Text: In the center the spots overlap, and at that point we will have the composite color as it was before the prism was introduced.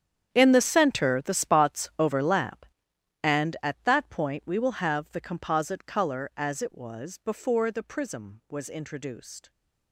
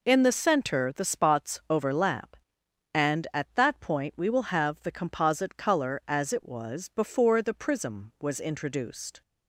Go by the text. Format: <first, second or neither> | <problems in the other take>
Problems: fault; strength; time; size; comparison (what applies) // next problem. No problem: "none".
second | gets quieter; strong; throughout; 16.5 dB